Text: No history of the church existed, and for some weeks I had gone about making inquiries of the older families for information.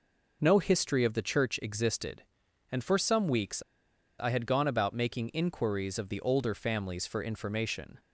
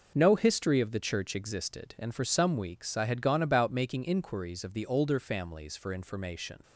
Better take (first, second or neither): second